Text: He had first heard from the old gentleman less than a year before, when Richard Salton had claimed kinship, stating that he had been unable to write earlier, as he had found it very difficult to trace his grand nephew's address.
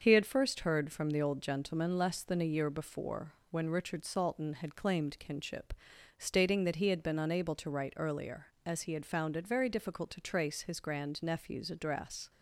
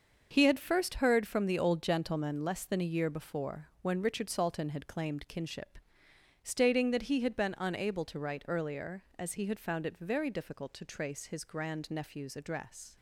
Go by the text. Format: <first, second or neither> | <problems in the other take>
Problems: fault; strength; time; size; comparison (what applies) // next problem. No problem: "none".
neither | starts louder than the rest; the same in both